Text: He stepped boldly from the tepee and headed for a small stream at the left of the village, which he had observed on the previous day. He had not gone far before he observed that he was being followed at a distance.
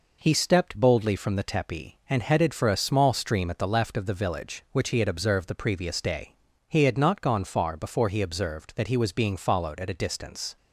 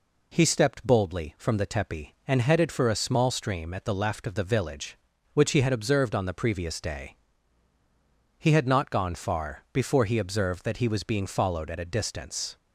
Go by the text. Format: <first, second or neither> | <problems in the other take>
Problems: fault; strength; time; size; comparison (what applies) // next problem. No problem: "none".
second | skips "on"; at 5.4 s